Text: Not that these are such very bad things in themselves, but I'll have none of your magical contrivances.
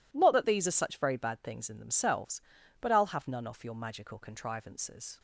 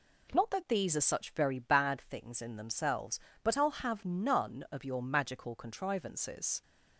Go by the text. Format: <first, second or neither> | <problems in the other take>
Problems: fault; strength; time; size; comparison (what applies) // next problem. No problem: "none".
second | says "off" for "of"; at 3.4 s